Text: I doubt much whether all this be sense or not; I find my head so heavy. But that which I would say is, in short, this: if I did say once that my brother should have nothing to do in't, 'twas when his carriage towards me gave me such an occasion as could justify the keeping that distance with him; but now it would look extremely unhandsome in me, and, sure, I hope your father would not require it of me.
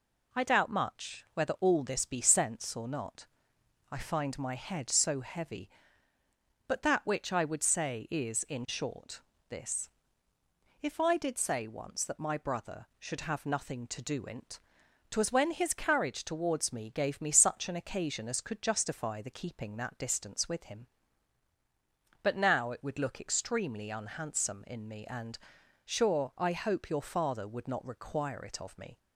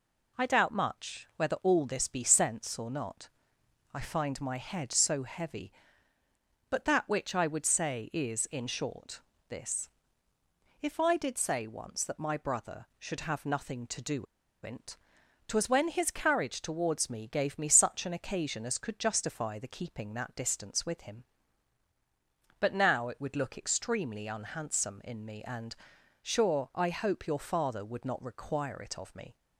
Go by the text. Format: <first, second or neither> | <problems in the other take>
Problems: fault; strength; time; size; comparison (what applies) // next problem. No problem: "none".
first | pauses between "do" and "in't"; at 14.2 s; 0.37 s long